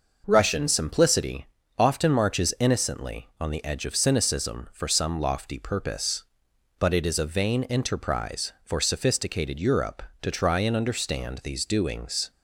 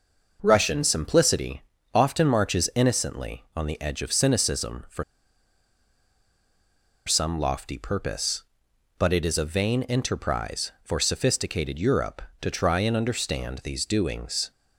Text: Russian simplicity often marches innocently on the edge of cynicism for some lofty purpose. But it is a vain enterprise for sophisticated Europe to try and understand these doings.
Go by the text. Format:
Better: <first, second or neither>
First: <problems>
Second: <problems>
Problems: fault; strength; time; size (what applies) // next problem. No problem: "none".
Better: first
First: pauses between "simplicity" and "often"; slight; at 1.4 s; 0.32 s long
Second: pauses between "simplicity" and "often"; slight; at 1.6 s; 0.32 s long // pauses between "for" and "some"; strong; at 5.0 s; 2.0 s long